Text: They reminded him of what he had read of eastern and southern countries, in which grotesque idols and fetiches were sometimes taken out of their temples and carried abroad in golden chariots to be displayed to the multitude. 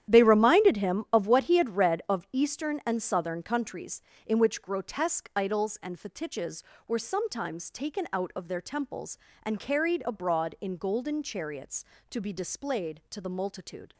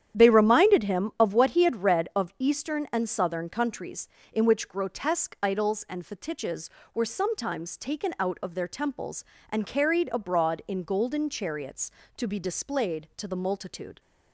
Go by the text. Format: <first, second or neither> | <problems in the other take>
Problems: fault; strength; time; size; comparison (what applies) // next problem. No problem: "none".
second | gets quieter; strong; throughout; 12 dB // starts louder than the rest; strong; until 1.1 s; 11 dB; strong in the second